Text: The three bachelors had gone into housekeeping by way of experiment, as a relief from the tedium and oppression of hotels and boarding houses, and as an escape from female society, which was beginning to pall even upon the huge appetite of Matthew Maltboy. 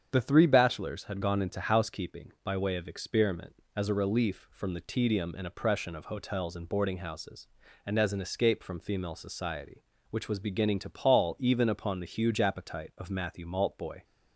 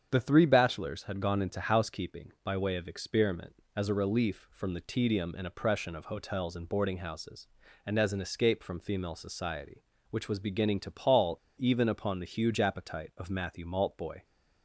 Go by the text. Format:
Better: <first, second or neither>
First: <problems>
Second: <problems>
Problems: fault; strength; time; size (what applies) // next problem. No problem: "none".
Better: first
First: starts louder than the rest; strong; until 1.1 s; 7.5 dB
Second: starts louder than the rest; strong; until 1.1 s; 7.5 dB // pauses between "pall" and "even"; slight; at 11.3 s; 0.20 s long